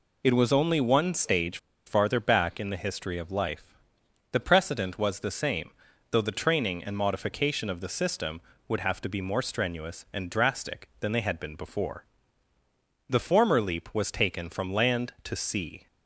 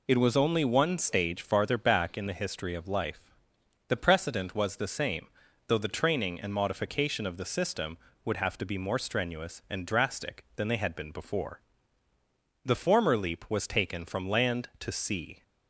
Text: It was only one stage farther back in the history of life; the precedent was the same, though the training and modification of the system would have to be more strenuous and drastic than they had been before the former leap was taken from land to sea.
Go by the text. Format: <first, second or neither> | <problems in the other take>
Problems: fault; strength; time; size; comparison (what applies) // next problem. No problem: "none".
second | pauses between "stage" and "farther"; slight; at 1.5 s; 0.28 s long // pauses between "before" and "the"; at 12.0 s; 1.0 s long; also in the second